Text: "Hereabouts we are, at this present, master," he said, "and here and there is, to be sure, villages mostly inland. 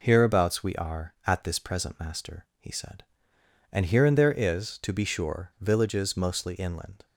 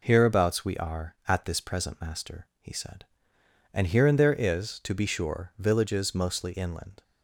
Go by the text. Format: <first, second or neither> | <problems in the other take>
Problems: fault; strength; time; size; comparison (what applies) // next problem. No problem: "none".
neither | none